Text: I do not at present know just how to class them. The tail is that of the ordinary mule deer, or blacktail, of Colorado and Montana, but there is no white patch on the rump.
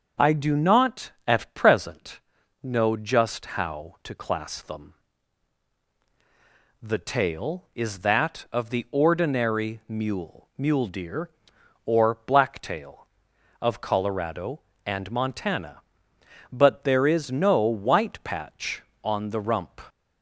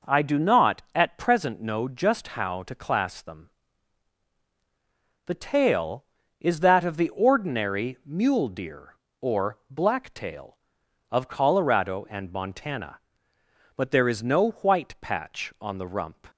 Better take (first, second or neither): second